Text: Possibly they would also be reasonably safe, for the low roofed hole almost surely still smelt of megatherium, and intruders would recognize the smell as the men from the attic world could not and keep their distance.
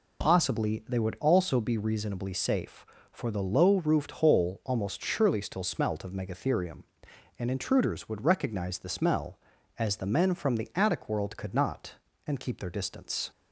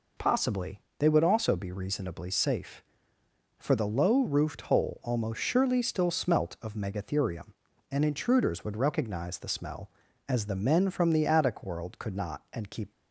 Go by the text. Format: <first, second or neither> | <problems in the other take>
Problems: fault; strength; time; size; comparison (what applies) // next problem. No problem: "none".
first | pauses between "Possibly" and "they"; slight; at 0.7 s; 0.18 s long // stops before "their distance"; at 12.9 s